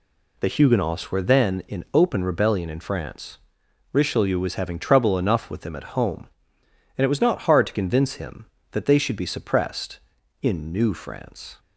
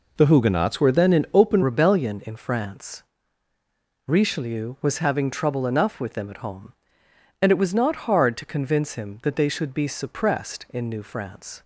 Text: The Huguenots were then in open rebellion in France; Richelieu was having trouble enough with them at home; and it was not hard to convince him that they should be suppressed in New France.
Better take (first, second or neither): first